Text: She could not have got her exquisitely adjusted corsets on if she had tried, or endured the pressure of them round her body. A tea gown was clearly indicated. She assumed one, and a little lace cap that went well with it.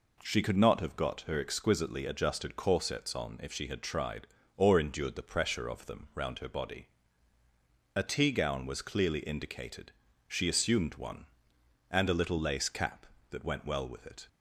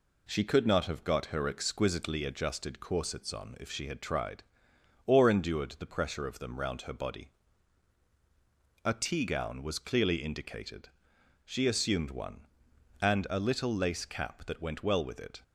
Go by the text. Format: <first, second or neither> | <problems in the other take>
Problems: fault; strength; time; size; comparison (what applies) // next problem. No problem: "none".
neither | none